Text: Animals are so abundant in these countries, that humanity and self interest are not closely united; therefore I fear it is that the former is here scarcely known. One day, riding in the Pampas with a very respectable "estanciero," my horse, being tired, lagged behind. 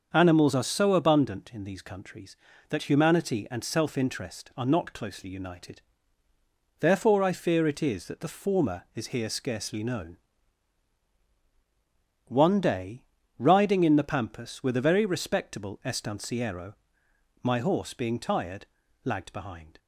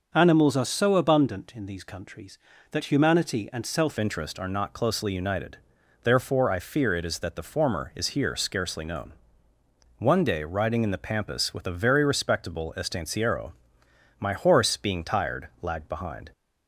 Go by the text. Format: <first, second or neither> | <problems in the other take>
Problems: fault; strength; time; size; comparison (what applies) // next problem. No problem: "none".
first | starts louder than the rest; noticeable; until 1.1 s; 6 dB; also in the first // changes voice at "interest"; from 3.9 s on; 12.3 s long